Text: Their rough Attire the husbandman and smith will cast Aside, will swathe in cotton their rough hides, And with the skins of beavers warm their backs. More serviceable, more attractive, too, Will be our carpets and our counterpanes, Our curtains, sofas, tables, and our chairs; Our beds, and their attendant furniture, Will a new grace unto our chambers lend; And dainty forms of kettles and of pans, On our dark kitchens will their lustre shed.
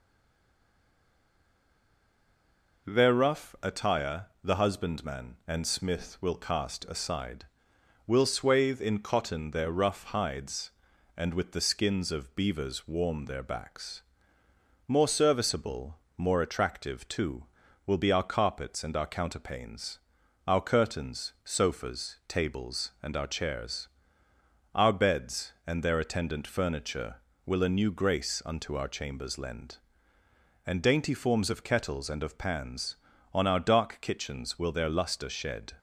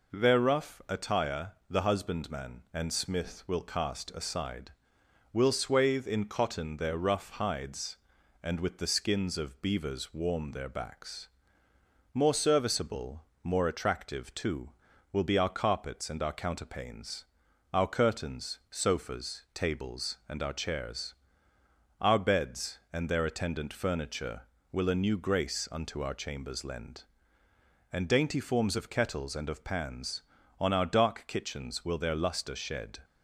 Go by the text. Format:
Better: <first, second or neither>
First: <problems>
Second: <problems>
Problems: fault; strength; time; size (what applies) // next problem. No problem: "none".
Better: second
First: stays silent before the first word; strong; until 2.8 s; 2.8 s long // pauses between "Attire" and "the"; slight; at 4.2 s; 0.16 s long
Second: pauses between "Attire" and "the"; slight; at 1.5 s; 0.16 s long